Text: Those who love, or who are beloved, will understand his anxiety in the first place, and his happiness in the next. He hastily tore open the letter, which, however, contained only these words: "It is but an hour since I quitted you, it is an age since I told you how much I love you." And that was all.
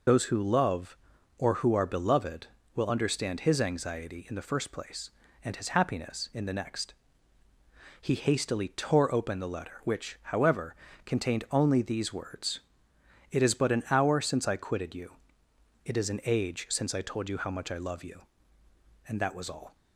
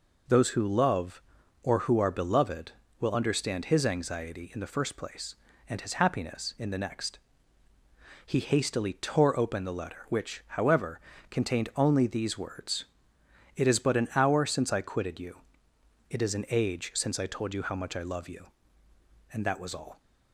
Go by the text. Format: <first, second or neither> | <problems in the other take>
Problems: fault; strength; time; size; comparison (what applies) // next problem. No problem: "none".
second | loses the start of "Those"; at 0.0 s; 45 ms